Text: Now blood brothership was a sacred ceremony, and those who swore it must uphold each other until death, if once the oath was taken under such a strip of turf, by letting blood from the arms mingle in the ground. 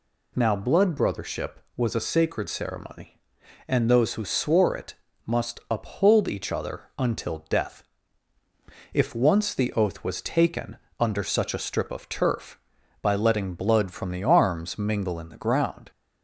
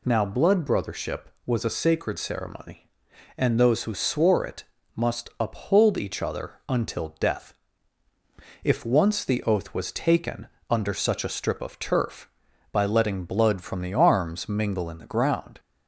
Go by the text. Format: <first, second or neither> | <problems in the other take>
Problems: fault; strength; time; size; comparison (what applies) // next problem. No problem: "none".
neither | pauses between "it" and "must"; slight; the same in both // pauses between "taken" and "under"; slight; the same in both